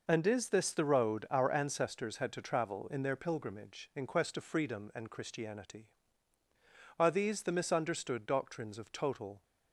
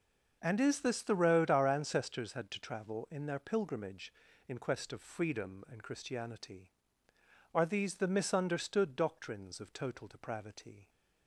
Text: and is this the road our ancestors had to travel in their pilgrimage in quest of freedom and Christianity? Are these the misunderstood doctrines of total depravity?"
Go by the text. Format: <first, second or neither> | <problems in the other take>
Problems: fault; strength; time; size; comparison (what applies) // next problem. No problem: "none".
second | stops before "depravity"; at 9.4 s